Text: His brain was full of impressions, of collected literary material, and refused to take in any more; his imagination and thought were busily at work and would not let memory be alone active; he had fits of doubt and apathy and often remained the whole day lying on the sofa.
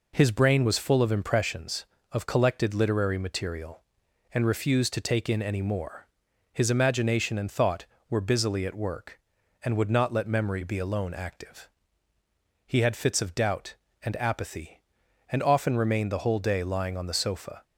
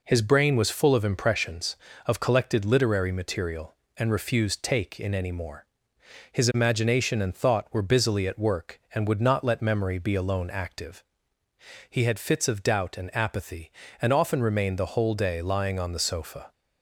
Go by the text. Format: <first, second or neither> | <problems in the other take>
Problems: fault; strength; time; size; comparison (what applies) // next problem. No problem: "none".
first | skips "to"; at 4.6 s